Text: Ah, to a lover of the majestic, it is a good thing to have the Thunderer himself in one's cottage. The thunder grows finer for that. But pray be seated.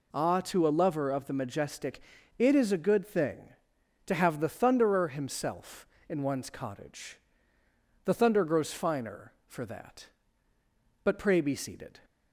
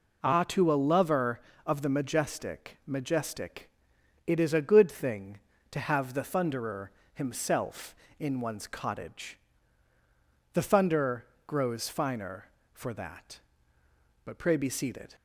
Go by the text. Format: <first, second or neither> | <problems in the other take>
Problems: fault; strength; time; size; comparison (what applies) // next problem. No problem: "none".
first | says "majestic" twice; at 2.8 s // pauses between "Thunderer" and "himself"; slight; at 6.9 s; 0.24 s long // pauses between "thunder" and "grows"; slight; at 11.2 s; 0.22 s long